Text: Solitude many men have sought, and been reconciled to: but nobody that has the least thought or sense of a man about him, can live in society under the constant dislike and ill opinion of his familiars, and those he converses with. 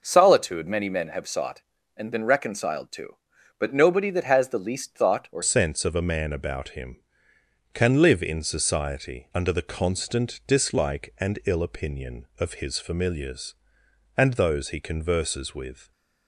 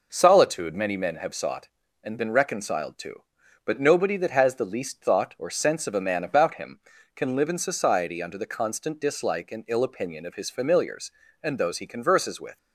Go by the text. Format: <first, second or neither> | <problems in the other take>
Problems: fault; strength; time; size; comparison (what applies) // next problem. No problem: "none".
second | changes voice at "sense"; from 5.4 s on; 10.5 s long